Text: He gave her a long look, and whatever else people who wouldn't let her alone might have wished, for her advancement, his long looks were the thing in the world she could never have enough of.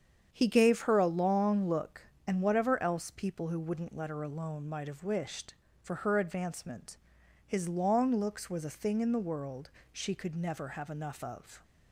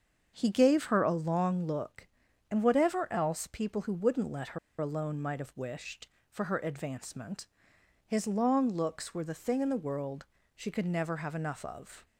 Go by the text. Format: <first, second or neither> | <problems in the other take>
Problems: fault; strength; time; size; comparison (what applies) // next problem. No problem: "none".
first | starts louder than the rest; until 1.3 s; 7 dB; strong in the first // pauses between "her" and "alone"; slight; at 4.5 s; 0.22 s long // pauses between "world" and "she"; slight; at 10.2 s; 0.28 s long; slight in the first